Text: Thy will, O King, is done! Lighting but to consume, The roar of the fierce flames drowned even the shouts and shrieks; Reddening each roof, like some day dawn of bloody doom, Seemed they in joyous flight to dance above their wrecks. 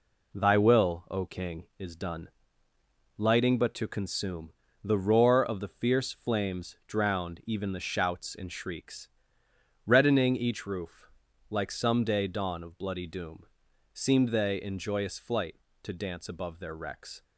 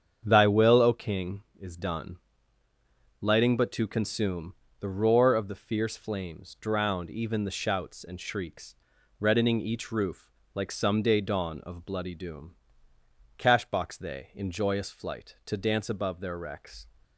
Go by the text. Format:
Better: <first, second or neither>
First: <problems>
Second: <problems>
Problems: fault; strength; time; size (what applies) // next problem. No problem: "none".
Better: first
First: none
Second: starts louder than the rest; strong; until 1.2 s; 7.5 dB // says "Cashbox" for "Seemed"; at 13.3 s